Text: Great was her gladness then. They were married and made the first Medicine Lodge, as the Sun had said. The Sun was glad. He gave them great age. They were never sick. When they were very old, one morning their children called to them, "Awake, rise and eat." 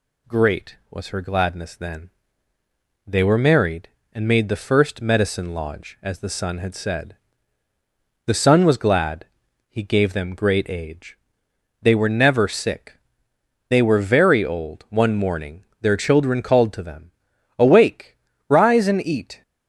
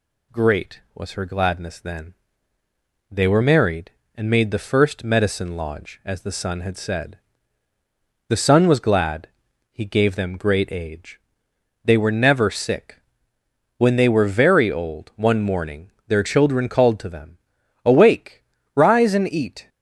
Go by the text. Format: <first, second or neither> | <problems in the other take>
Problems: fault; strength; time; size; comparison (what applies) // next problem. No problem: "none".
second | skips "When"; at 13.3 s // pauses between "morning" and "their"; slight; at 15.6 s; 0.16 s long; slight in the second